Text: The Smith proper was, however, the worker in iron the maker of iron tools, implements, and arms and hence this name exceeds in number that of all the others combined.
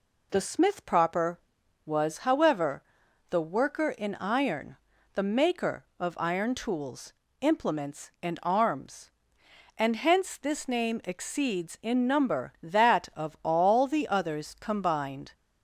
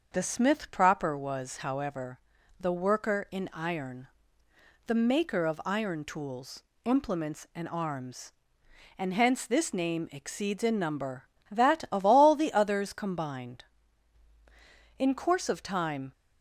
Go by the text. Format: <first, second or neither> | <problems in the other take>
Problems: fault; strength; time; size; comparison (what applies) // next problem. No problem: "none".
first | starts louder than the rest; until 1.1 s; 6.5 dB // pauses between "iron" and "the"; noticeable; at 4.0 s; 0.80 s long; also in the first // goes on to say "In course of time"; noticeable; from 14.9 s on; 1.1 s long